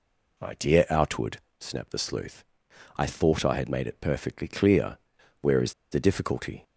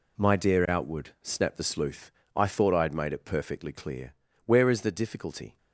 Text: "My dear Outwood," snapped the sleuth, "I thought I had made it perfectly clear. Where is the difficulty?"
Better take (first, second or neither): second